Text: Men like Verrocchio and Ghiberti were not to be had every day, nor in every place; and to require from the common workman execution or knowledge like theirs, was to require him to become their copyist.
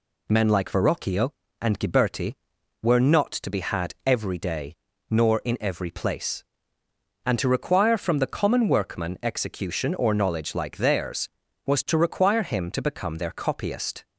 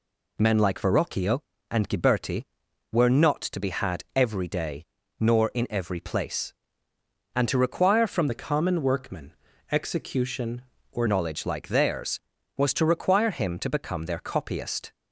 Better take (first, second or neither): first